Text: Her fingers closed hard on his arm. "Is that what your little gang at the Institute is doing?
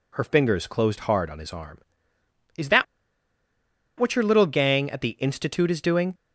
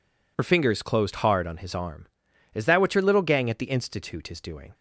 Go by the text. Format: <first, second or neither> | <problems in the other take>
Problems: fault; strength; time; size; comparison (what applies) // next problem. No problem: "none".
second | pauses between "that" and "what"; at 2.8 s; 1.1 s long